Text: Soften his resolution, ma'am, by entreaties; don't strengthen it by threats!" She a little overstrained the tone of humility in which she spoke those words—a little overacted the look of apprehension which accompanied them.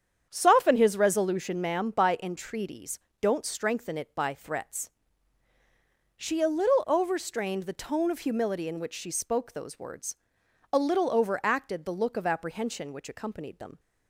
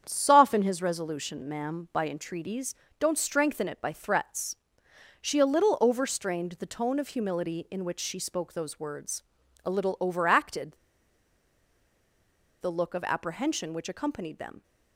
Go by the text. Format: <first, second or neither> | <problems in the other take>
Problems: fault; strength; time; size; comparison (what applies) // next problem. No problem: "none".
first | starts louder than the rest; strong; until 1.0 s; 8 dB; strong in the first // pauses between "overacted" and "the"; strong; at 10.7 s; 1.8 s long